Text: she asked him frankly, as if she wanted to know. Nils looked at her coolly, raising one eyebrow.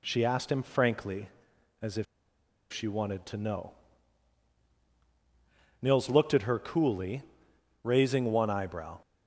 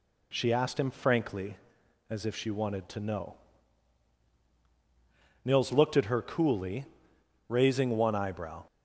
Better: second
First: pauses between "if" and "she"; noticeable; at 2.0 s; 0.66 s long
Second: none

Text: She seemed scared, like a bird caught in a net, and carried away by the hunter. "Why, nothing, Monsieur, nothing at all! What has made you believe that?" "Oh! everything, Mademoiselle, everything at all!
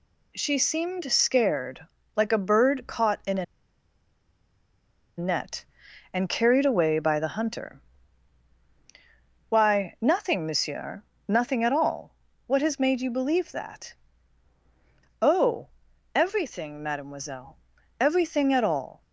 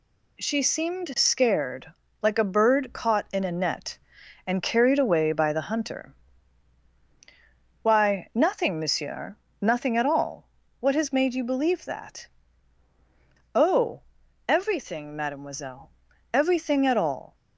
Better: second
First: pauses between "a" and "net"; strong; at 3.4 s; 1.7 s long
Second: none

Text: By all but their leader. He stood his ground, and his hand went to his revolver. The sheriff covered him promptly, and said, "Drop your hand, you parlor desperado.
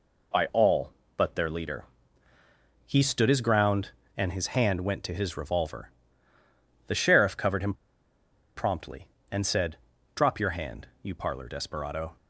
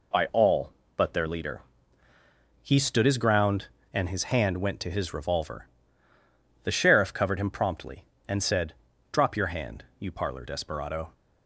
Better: second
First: pauses between "him" and "promptly"; noticeable; at 7.7 s; 0.81 s long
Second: none

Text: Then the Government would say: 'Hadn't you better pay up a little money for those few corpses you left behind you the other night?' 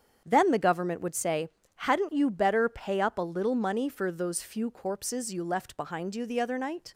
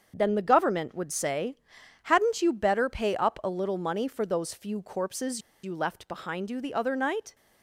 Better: first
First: starts louder than the rest; strong; until 1.2 s; 8 dB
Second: starts louder than the rest; strong; until 1.1 s; 7 dB // pauses between "corpses" and "you"; slight; at 5.4 s; 0.23 s long

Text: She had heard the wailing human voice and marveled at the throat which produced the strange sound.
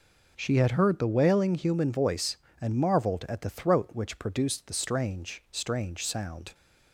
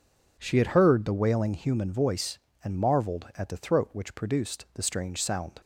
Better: second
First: says "strange" twice; at 5.4 s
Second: none

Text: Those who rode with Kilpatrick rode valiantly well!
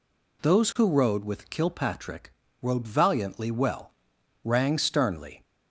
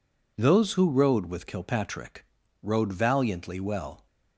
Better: second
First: pauses between "Kilpatrick" and "rode"; slight; at 2.3 s; 0.28 s long // goes on to say "Rang sternly"; noticeable; from 4.4 s on; 1.0 s long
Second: pauses between "Kilpatrick" and "rode"; at 2.2 s; 0.38 s long

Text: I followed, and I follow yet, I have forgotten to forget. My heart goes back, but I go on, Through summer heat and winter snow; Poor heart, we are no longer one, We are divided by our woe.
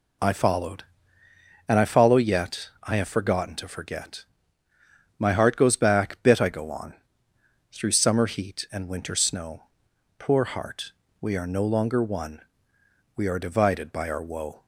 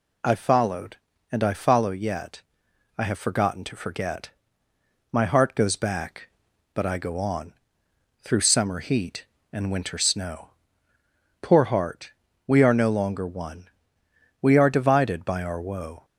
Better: second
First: says "bit" for "but"; at 6.2 s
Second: none

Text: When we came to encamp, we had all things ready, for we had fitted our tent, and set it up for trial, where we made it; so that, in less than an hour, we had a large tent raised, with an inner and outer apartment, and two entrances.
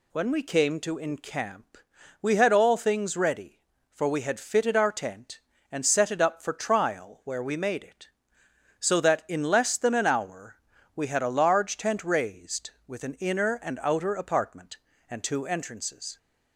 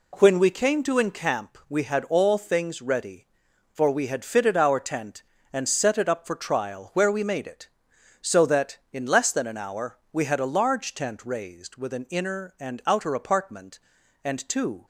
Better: first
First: none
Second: stops before "entrances"; at 14.8 s

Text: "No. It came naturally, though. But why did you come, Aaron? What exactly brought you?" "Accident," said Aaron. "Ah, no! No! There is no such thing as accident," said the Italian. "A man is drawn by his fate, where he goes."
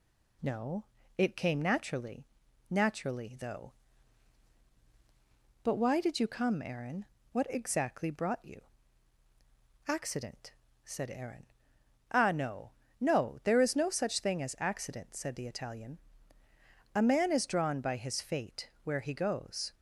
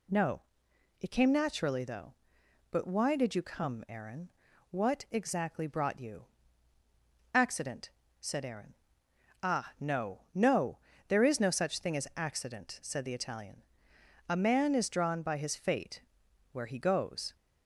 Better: second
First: says "naturally" twice; at 2.6 s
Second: none

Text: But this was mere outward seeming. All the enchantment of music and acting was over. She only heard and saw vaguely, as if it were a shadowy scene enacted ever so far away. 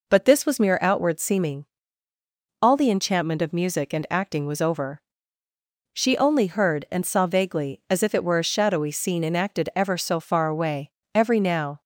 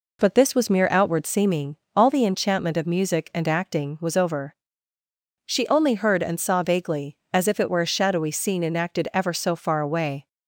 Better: second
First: goes on to say "Every now"; noticeable; from 11.1 s on; 0.66 s long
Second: none

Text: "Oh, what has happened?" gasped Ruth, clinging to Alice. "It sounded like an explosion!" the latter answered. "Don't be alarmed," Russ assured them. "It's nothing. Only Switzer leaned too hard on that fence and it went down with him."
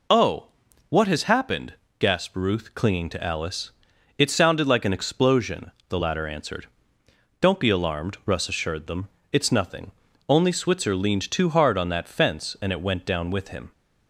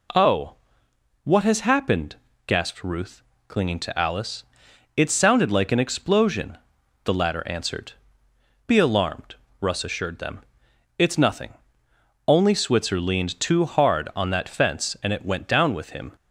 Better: first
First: none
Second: skips "Don't"; at 8.3 s

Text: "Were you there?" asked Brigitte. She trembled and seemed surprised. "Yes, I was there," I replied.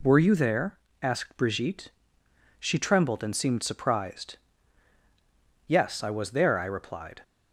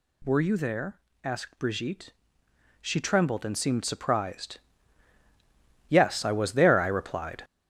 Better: first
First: none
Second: gets louder; strong; throughout; 8.5 dB

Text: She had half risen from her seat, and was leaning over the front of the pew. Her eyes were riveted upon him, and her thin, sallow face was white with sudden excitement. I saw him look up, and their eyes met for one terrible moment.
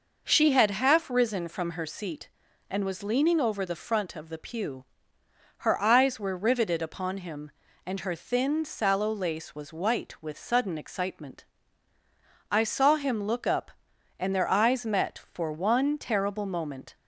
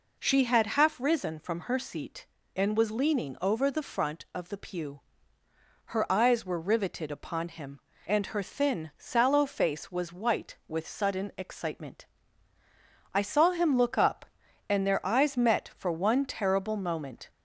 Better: second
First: says "lace" for "face"; at 9.1 s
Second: none

